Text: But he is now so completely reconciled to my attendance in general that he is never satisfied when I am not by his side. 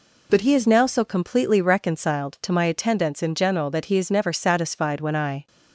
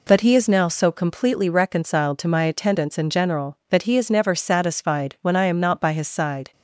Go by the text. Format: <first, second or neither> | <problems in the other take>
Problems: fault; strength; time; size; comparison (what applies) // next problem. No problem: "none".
second | stops before "am not by his side"; at 5.4 s